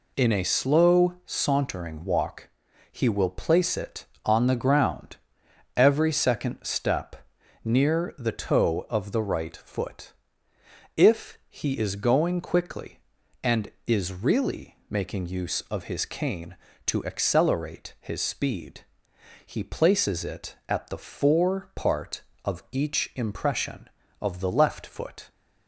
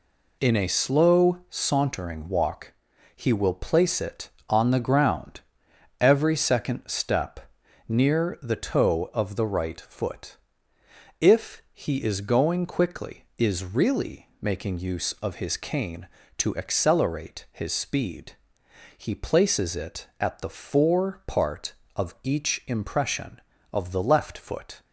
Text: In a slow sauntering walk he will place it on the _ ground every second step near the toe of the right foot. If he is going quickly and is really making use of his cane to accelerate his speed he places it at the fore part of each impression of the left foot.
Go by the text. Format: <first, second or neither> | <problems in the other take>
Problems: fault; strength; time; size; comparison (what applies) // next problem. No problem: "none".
first | pauses between "walk" and "he"; at 2.7 s; 0.44 s long; also in the first // pauses between "ground" and "every"; noticeable; at 5.4 s; 0.60 s long; noticeable in the first // pauses between "step" and "near"; noticeable; at 7.4 s; 0.48 s long; noticeable in the first // skips "and"; at 13.3 s // pauses between "speed" and "he"; noticeable; at 18.3 s; 0.62 s long; noticeable in the first